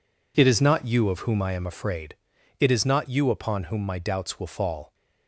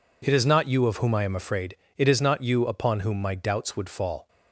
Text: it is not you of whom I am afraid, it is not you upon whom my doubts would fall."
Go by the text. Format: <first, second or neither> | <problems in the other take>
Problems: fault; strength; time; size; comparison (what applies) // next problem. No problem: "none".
second | says "will" for "would"; at 4.4 s